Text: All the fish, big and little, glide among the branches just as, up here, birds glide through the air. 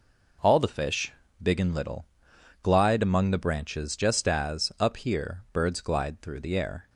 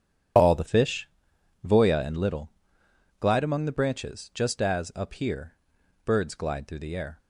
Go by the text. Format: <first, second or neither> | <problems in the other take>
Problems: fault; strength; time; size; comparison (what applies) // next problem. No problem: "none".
first | says "voya" for "big"; at 1.6 s